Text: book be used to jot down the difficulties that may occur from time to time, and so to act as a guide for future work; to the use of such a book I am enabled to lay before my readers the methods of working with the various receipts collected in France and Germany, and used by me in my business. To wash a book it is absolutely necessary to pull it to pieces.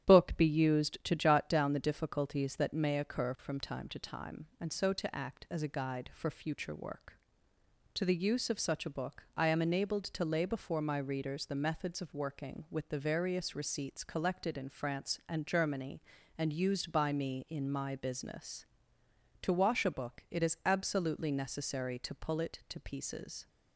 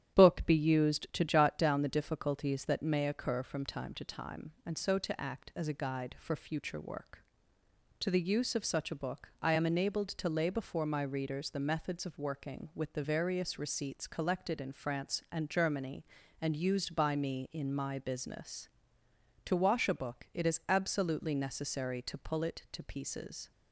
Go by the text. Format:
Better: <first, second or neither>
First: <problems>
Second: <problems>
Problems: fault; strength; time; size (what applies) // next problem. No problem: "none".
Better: neither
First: starts louder than the rest; strong; until 1.0 s; 10.5 dB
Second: starts louder than the rest; strong; until 1.1 s; 10.5 dB